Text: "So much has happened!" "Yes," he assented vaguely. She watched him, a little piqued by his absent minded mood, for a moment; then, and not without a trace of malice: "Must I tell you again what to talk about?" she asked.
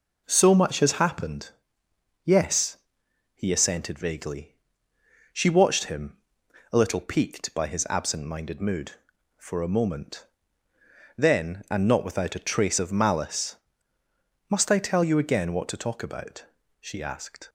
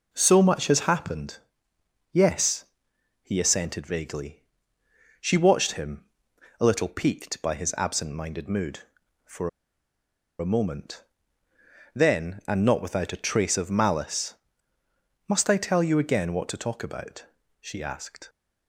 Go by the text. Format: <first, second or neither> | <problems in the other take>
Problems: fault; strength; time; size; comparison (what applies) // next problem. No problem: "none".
first | pauses between "for" and "a"; noticeable; at 9.4 s; 0.90 s long